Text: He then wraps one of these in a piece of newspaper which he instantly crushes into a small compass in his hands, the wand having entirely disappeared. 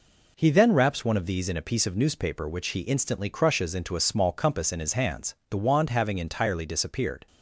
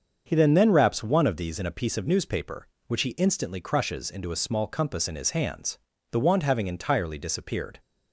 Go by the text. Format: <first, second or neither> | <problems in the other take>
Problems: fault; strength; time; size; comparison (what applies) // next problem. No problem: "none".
first | starts louder than the rest; until 1.2 s; 7 dB // says "then" twice; at 0.5 s